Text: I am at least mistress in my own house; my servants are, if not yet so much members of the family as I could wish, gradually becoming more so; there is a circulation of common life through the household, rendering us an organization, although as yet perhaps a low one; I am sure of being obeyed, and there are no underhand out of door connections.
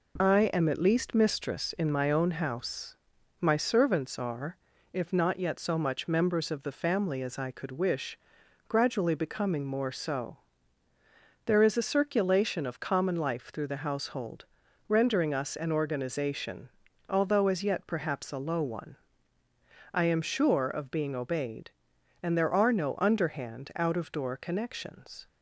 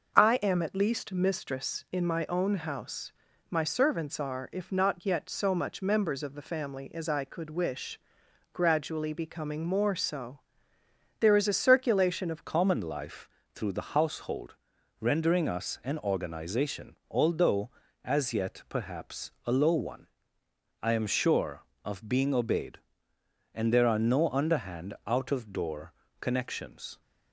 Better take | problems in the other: first | starts louder than the rest; until 1.2 s; 6 dB // changes voice at "common"; from 12.4 s on; 14.6 s long // pauses between "life" and "through"; slight; at 13.2 s; 0.24 s long // pauses between "door" and "connections"; slight; at 25.9 s; 0.28 s long

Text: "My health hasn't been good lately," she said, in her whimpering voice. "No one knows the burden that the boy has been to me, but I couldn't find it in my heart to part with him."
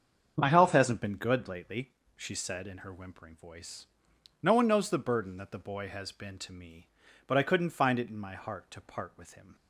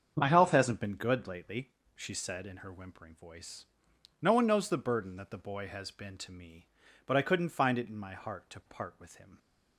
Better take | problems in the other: neither | starts louder than the rest; strong; the same in both

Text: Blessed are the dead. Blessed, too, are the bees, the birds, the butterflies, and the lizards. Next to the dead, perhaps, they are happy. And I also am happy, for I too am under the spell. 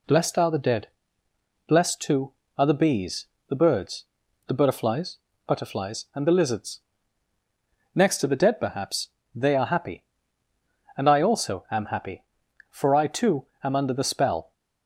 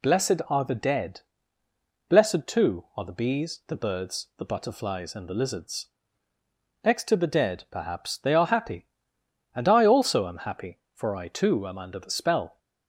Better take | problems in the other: second | says "butterflies" twice; at 5.4 s // pauses between "too" and "am"; slight; at 13.4 s; 0.18 s long

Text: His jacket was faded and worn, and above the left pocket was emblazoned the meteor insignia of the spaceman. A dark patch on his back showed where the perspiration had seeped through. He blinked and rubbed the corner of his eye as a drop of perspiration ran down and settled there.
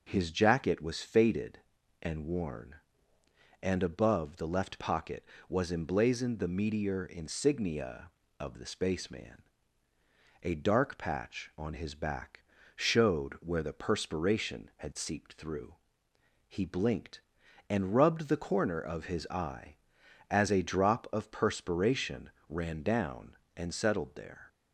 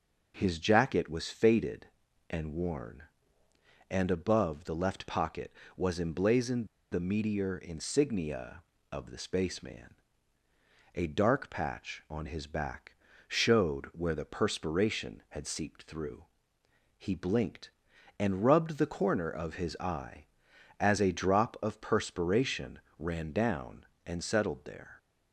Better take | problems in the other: first | pauses between "emblazoned" and "the"; slight; at 6.6 s; 0.24 s long // pauses between "back" and "showed"; slight; at 12.9 s; 0.30 s long; slight in the first // pauses between "perspiration" and "ran"; slight; at 22.7 s; 0.18 s long; slight in the first

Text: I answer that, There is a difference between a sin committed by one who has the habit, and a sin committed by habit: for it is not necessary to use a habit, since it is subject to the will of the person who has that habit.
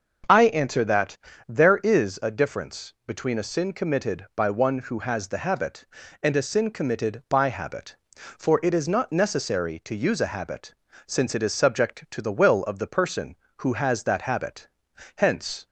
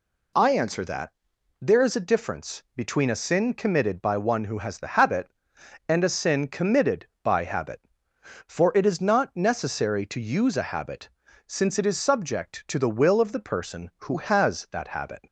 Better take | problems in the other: second | starts louder than the rest; strong; until 1.6 s; 7.5 dB // goes on to say "Hence"; from 15.1 s on; 0.50 s long

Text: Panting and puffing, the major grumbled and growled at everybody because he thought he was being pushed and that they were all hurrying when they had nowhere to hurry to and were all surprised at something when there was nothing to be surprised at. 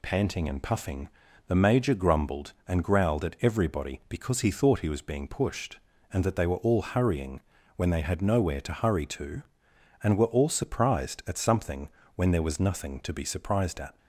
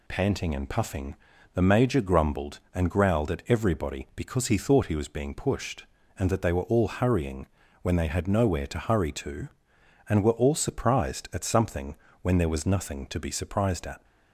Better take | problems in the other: neither | pauses between "hurrying" and "when"; slight; the same in both // pauses between "something" and "when"; slight; the same in both

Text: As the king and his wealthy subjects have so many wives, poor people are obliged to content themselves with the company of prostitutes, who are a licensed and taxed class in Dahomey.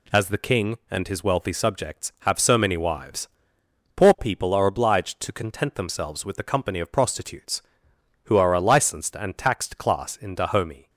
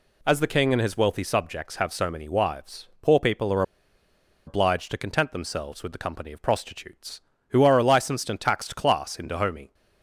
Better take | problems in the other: first | pauses between "are" and "obliged"; noticeable; at 3.6 s; 0.84 s long

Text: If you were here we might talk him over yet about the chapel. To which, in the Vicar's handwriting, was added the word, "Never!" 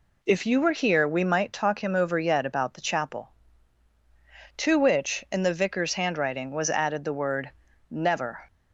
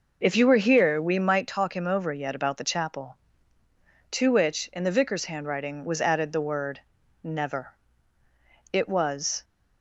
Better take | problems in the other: first | goes on to say "It was"; noticeable; from 8.7 s on; 0.72 s long

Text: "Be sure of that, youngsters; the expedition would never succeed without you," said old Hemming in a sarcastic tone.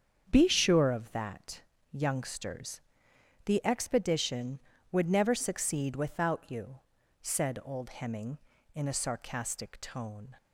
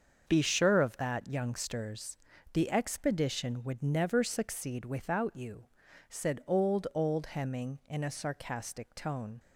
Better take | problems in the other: first | starts louder than the rest; until 1.2 s; 7 dB; strong in the first // says "old" twice; at 6.9 s

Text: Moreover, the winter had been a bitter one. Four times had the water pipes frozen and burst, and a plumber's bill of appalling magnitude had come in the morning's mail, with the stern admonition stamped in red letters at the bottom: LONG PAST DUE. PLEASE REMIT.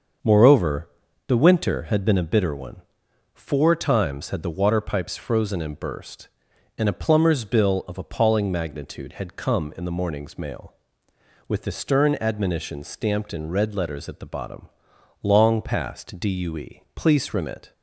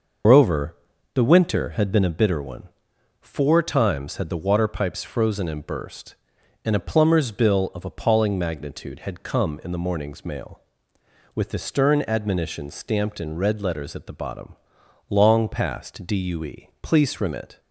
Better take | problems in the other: first | loses the start of "Moreover"; at 0.2 s; 160 ms // starts louder than the rest; noticeable; until 1.6 s; 6 dB; also in the first

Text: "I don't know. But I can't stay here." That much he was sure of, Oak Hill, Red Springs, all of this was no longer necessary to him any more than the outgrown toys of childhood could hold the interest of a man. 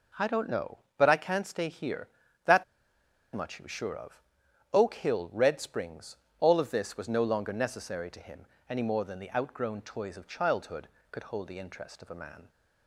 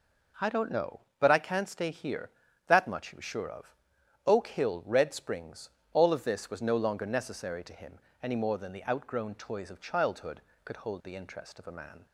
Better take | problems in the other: second | pauses between "That" and "much"; noticeable; at 2.6 s; 0.70 s long // pauses between "him" and "any"; slight; at 8.4 s; 0.20 s long; slight in the second

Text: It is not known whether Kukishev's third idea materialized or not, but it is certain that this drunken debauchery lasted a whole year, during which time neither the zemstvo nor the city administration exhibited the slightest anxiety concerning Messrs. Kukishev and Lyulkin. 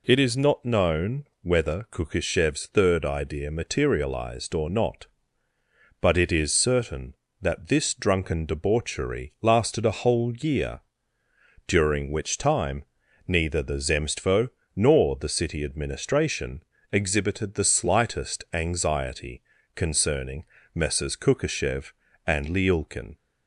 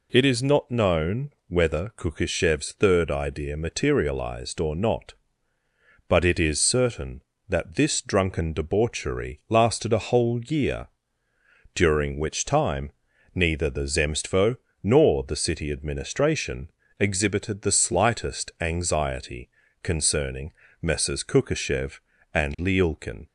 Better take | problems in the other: neither | pauses between "time" and "neither"; the same in both // pauses between "zemstvo" and "nor"; slight; the same in both // pauses between "administration" and "exhibited"; slight; the same in both // pauses between "anxiety" and "concerning"; slight; the same in both // pauses between "concerning" and "Messrs"; slight; the same in both

